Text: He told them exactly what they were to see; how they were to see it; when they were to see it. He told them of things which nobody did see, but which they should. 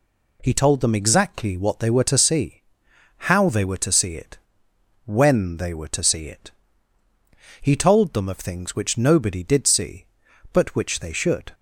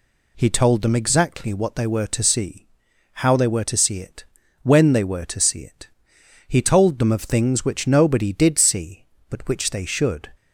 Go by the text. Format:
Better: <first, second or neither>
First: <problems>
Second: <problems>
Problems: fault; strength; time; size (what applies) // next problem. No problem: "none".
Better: neither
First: none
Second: none